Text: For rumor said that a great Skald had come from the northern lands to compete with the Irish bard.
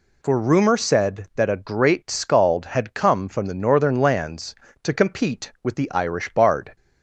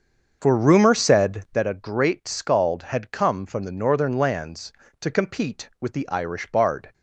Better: first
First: none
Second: starts louder than the rest; until 1.7 s; 7 dB

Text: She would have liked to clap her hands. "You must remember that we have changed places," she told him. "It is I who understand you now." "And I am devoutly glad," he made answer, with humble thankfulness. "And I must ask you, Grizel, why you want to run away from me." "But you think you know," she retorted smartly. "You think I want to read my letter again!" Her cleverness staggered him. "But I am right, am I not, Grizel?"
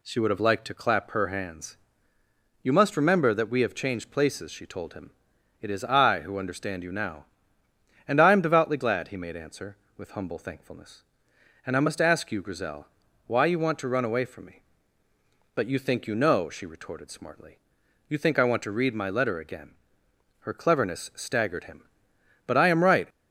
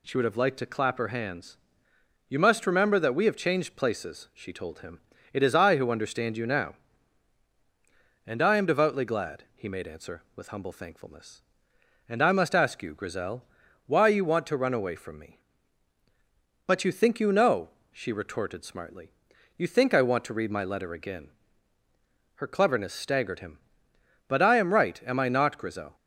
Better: second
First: stops before "am I not Grizel"; at 23.1 s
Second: none

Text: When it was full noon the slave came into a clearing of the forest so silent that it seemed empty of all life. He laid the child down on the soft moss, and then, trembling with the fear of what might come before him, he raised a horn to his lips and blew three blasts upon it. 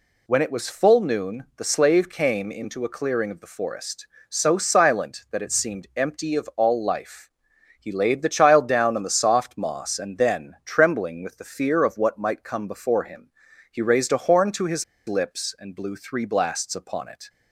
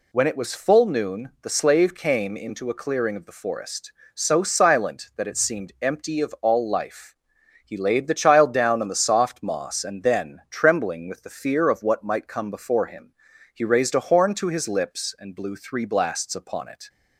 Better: second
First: pauses between "his" and "lips"; slight; at 14.8 s; 0.22 s long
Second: none

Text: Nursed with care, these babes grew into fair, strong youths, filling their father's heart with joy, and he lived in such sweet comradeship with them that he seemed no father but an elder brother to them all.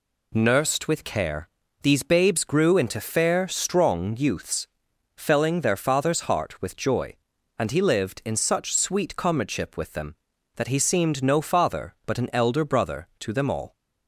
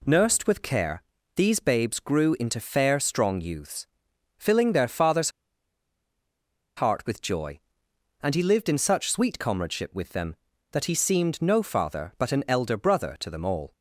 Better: first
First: none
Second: pauses between "father's" and "heart"; strong; at 5.2 s; 1.4 s long

